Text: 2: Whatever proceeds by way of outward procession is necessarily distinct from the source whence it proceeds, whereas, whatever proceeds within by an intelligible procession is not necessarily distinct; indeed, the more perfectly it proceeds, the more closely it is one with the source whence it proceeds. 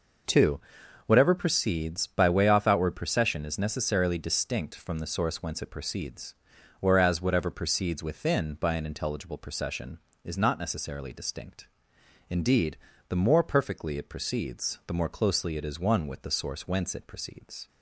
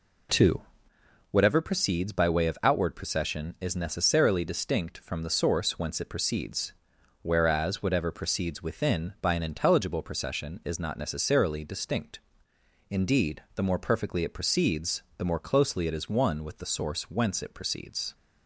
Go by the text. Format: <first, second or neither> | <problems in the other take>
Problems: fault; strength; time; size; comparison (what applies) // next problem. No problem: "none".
second | says "off" for "of"; at 2.4 s